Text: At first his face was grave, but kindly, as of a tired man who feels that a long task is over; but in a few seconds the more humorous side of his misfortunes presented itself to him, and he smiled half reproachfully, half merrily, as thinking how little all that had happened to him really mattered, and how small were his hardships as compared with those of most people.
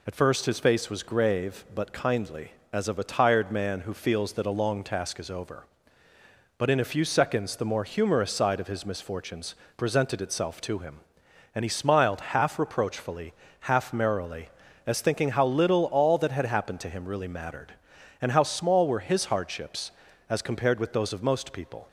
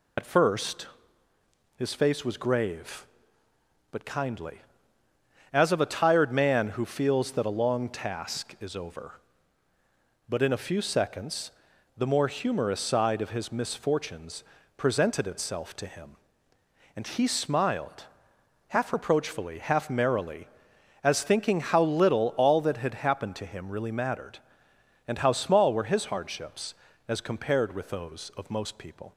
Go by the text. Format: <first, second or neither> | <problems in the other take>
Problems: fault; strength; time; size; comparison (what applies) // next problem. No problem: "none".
first | loses the start of "At"; at 0.1 s; 65 ms // pauses between "first" and "his"; noticeable; at 0.8 s; 0.88 s long // pauses between "seconds" and "the"; noticeable; at 11.4 s; 0.48 s long // pauses between "misfortunes" and "presented"; slight; at 14.4 s; 0.34 s long; slight in the first // pauses between "smiled" and "half"; noticeable; at 18.0 s; 0.62 s long